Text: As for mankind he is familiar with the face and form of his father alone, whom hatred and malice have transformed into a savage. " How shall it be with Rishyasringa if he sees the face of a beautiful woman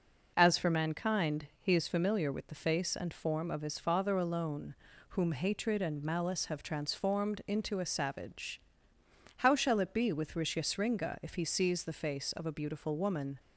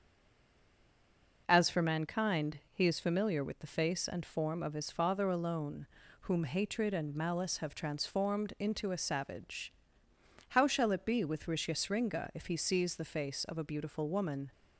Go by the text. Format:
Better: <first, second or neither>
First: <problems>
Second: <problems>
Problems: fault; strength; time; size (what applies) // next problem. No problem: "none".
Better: first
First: starts louder than the rest; strong; until 1.3 s; 7.5 dB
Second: stays silent before the first word; noticeable; until 1.4 s; 1.4 s long // starts louder than the rest; strong; until 2.4 s; 7.5 dB